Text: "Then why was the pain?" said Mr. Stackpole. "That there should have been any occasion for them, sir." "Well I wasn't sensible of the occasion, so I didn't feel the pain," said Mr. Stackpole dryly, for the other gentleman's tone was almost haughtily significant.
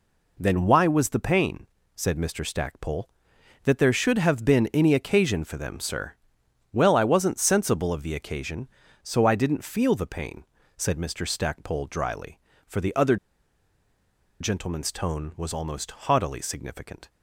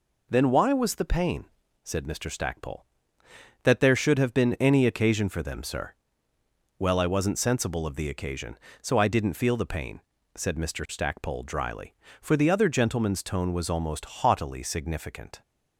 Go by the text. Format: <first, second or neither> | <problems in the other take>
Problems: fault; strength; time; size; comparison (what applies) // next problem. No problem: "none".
second | pauses between "other" and "gentleman's"; at 13.1 s; 1.2 s long